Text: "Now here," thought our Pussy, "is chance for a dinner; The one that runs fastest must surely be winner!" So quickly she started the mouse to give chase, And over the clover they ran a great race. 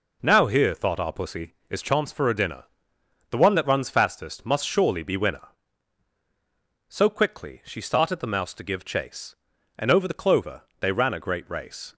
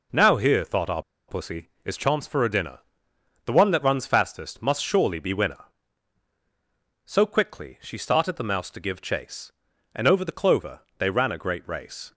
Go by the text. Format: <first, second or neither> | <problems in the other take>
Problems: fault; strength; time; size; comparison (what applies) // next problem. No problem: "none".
first | pauses between "our" and "Pussy"; slight; at 1.0 s; 0.26 s long // pauses between "clover" and "they"; slight; at 10.8 s; 0.18 s long; slight in the first